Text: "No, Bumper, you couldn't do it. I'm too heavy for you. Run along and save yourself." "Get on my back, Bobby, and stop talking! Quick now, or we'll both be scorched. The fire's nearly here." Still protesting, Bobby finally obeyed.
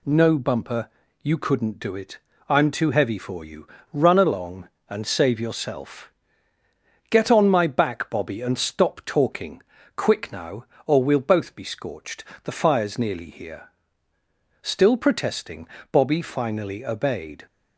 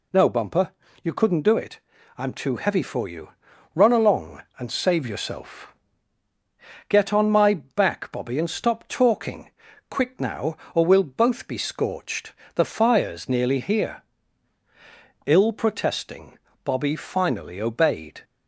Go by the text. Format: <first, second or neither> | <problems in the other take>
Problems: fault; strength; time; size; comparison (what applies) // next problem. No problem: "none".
first | says "Ill" for "Still"; at 15.2 s